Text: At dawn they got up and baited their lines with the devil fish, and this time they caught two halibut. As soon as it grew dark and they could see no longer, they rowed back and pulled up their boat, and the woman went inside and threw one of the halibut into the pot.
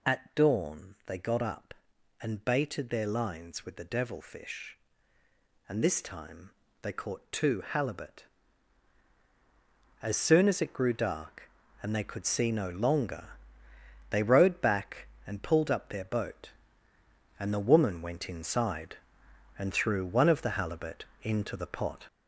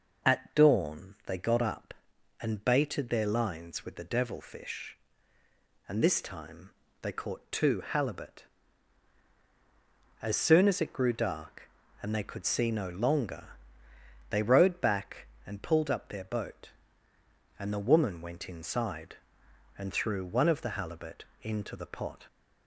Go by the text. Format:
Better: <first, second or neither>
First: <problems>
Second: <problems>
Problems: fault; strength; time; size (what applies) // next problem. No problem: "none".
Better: second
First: gets louder; noticeable; throughout; 5 dB // pauses between "time" and "they"; slight; at 6.5 s; 0.30 s long // pauses between "halibut" and "into"; slight; at 21.0 s; 0.18 s long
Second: pauses between "time" and "they"; slight; at 6.7 s; 0.30 s long // pauses between "halibut" and "into"; slight; at 21.2 s; 0.18 s long